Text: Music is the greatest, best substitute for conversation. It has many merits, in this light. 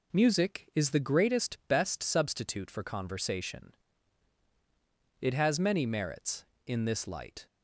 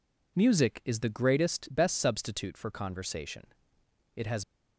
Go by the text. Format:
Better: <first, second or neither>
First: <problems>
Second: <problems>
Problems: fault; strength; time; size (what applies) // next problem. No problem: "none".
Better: first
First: none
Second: stops before "many merits in this light"; at 4.4 s